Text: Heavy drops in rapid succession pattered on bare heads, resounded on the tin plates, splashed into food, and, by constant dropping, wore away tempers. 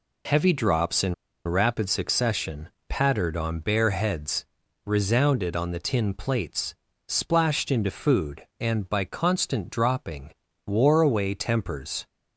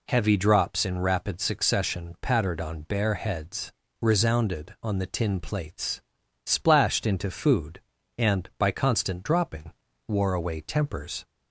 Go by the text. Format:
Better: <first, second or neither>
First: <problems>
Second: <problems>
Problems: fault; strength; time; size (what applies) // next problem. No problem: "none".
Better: second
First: pauses between "in" and "rapid"; slight; at 1.1 s; 0.32 s long // pauses between "succession" and "pattered"; slight; at 2.6 s; 0.20 s long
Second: none